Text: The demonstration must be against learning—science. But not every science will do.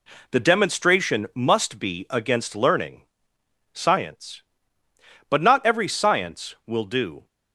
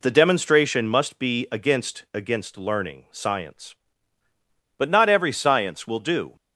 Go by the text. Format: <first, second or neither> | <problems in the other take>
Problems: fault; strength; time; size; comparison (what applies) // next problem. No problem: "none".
first | says "against" twice; at 2.1 s